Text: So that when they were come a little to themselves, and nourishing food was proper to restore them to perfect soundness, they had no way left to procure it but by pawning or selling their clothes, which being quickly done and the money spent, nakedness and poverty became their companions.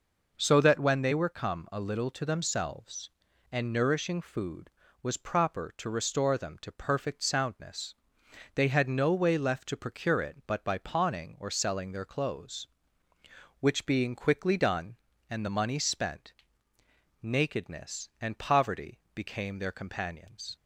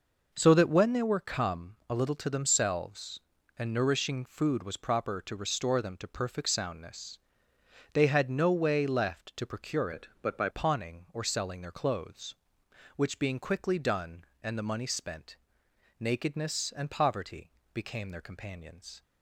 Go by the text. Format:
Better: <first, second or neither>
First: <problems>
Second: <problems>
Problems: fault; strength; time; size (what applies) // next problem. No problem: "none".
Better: first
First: none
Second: changes voice from "it" to "by"; from 9.9 to 10.4 s; 0.5 s long // pauses between "poverty" and "became"; slight; at 17.4 s; 0.24 s long